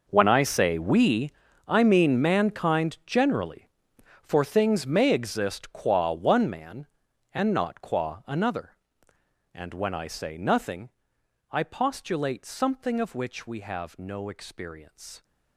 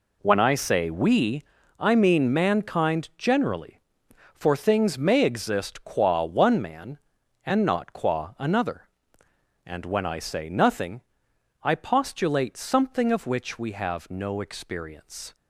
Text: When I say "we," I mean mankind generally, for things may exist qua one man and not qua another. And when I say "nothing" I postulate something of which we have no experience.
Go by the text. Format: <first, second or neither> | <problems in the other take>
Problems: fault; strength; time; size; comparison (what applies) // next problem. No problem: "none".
second | gets quieter; strong; throughout; 17 dB // pauses between "nothing" and "I"; noticeable; at 10.9 s; 0.60 s long; noticeable in the second